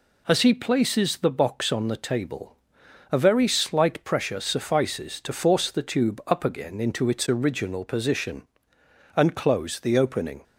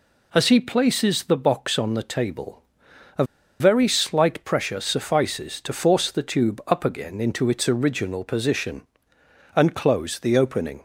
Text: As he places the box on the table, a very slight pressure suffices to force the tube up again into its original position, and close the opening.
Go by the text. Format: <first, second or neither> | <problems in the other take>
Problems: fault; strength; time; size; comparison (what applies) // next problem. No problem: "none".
first | pauses between "a" and "very"; slight; at 3.2 s; 0.35 s long